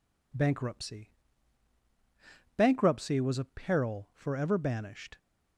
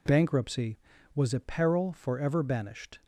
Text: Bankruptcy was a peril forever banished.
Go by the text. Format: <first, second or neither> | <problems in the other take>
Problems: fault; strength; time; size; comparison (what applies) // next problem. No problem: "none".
second | says "Bankruptcy" twice; at 2.5 s